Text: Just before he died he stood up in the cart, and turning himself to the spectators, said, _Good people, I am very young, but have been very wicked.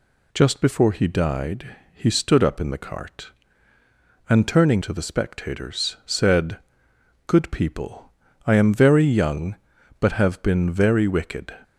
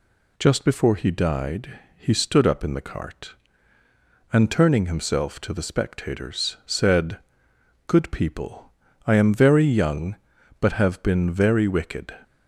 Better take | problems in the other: second | pauses between "died" and "he"; slight; at 1.7 s; 0.18 s long; slight in the second // skips "himself"; at 4.8 s

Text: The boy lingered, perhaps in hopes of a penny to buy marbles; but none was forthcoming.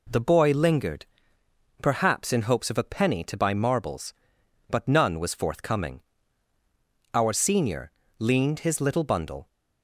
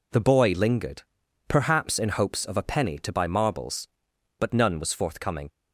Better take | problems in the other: second | goes on to say "Our senior leaned his little bundle"; strong; from 7.1 s on; 2.3 s long

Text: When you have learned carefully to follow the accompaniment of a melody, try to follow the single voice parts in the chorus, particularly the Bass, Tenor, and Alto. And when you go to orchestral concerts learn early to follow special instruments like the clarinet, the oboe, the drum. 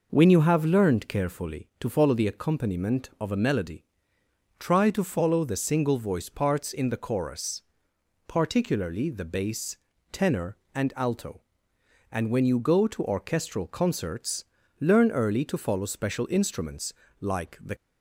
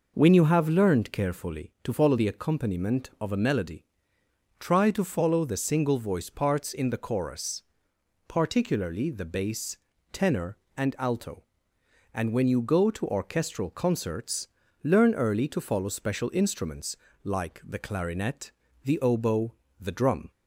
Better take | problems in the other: second | pauses between "concerts" and "learn"; slight; at 14.4 s; 0.34 s long; slight in the second // pauses between "instruments" and "like"; slight; at 16.9 s; 0.26 s long; slight in the second // stops before "clarinet the oboe the drum"; at 17.7 s

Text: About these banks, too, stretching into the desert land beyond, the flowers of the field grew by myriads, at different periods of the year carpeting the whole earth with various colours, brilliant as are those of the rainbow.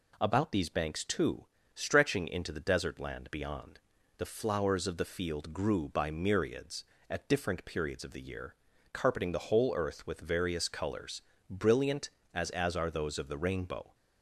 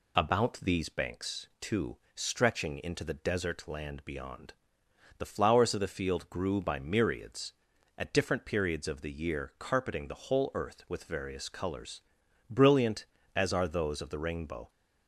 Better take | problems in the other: second | pauses between "year" and "carpeting"; at 8.5 s; 0.40 s long // says "as" twice; at 12.5 s

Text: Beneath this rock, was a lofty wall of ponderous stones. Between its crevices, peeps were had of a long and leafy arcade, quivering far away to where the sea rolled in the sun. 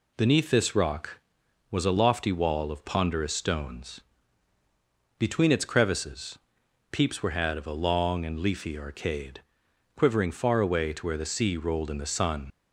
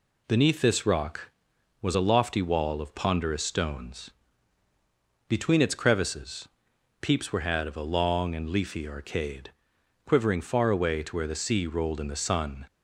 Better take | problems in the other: second | leaves "sun" unfinished; at 12.5 s; 60 ms

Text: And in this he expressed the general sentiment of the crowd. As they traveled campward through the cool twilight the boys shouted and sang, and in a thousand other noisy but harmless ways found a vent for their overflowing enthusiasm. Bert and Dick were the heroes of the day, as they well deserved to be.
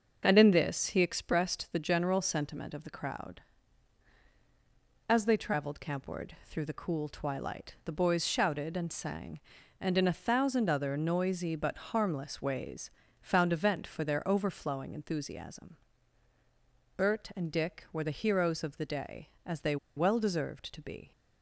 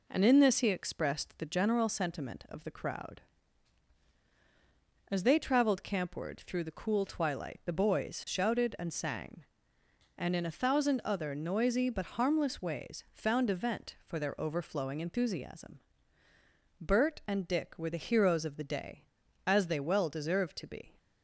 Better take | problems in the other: second | starts louder than the rest; until 1.2 s; 6.5 dB // pauses between "campward" and "through"; slight; at 6.3 s; 0.16 s long // pauses between "ways" and "found"; slight; at 12.8 s; 0.30 s long // pauses between "they" and "well"; slight; at 19.7 s; 0.20 s long

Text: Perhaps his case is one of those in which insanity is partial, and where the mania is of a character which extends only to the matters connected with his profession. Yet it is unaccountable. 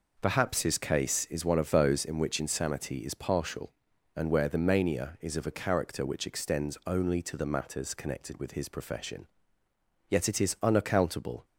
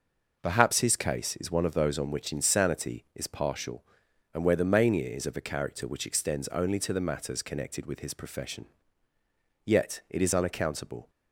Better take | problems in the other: first | says "on" for "in"; at 1.9 s

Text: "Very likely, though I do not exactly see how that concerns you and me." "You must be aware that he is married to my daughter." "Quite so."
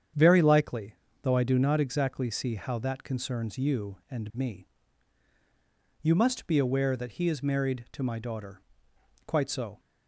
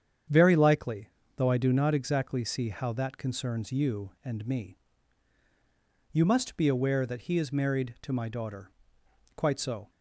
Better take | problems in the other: neither | starts louder than the rest; strong; the same in both

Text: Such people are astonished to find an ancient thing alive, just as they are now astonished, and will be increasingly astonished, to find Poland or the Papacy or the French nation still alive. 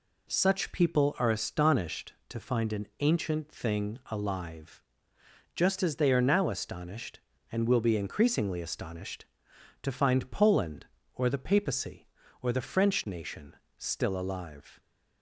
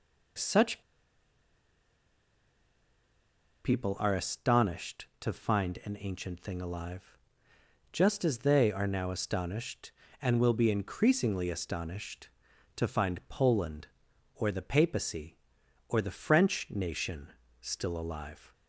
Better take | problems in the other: first | pauses between "Such" and "people"; strong; at 0.8 s; 2.8 s long // pauses between "nation" and "still"; slight; at 17.3 s; 0.26 s long; slight in the first

